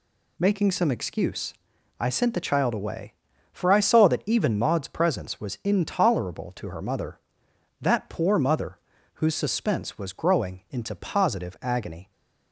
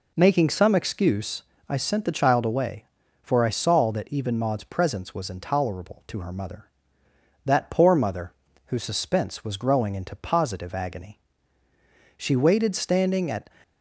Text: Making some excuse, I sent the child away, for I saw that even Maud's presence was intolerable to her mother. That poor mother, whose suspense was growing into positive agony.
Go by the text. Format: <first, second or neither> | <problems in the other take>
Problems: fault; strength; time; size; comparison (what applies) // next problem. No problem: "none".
first | goes on to say "She waited standing at"; from 12.1 s on; 1.3 s long